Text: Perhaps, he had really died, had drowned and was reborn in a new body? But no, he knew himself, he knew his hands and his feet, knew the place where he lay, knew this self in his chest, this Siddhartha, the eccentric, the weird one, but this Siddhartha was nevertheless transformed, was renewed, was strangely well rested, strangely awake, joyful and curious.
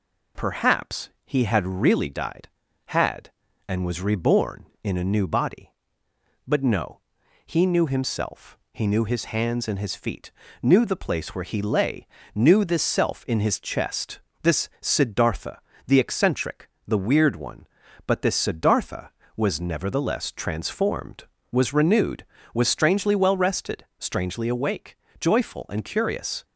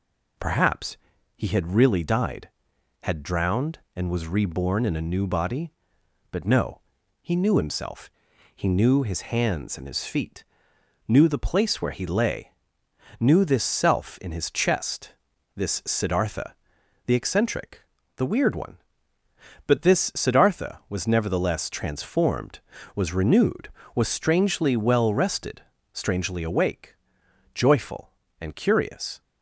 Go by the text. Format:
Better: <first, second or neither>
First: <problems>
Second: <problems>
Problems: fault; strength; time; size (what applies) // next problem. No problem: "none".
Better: second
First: skips "drowned"; at 3.4 s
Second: none